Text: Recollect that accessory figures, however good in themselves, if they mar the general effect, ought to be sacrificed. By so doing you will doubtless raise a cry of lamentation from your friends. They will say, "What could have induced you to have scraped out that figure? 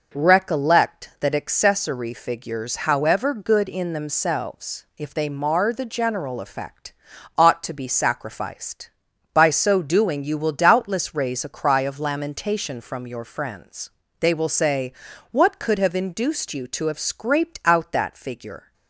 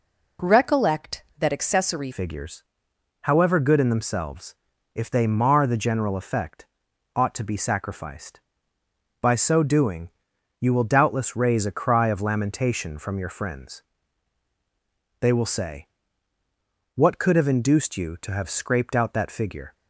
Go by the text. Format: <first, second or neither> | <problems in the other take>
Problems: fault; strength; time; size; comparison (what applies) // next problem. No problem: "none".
first | changes voice at "figures"; from 2.1 s on; 17.6 s long // pauses between "doing" and "you"; noticeable; at 10.0 s; 0.50 s long